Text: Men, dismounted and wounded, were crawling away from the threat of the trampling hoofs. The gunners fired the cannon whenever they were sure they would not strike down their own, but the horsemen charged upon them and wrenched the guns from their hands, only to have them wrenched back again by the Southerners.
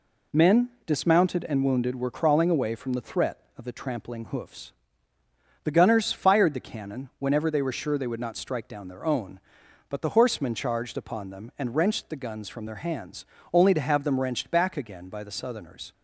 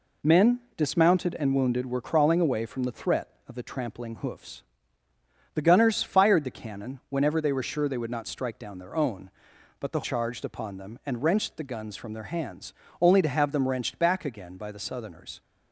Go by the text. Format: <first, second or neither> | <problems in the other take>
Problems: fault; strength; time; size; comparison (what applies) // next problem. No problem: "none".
first | skips "horsemen"; at 10.0 s